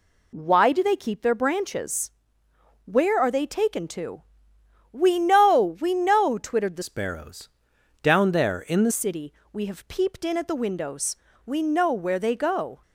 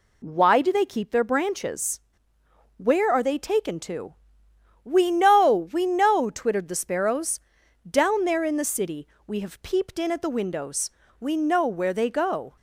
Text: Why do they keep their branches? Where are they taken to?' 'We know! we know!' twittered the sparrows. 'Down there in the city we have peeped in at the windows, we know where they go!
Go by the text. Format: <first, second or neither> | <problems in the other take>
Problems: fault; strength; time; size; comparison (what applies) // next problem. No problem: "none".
second | changes voice from "sparrows" to "the"; from 6.8 to 8.9 s; 2.1 s long // pauses between "city" and "we"; slight; at 9.3 s; 0.22 s long; slight in the second